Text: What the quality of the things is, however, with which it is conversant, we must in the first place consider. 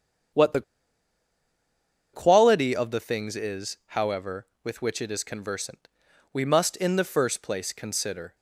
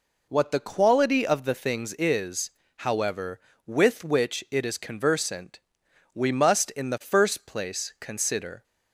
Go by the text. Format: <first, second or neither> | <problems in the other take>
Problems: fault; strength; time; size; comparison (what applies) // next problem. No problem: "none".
second | starts louder than the rest; strong; until 2.8 s; 8 dB // pauses between "the" and "quality"; strong; at 0.6 s; 1.5 s long